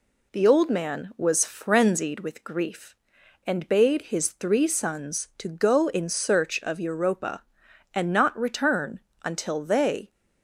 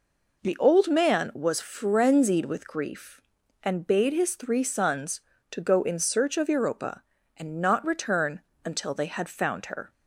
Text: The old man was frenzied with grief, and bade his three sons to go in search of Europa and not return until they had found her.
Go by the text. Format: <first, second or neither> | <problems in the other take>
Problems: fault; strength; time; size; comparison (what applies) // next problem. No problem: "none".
second | pauses between "return" and "until"; slight; at 8.9 s; 0.26 s long; slight in the second // stops before "had found her"; at 10.1 s